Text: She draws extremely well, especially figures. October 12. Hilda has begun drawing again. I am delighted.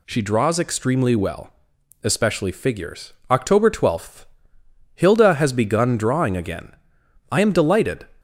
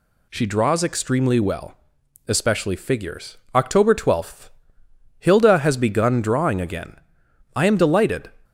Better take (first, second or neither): neither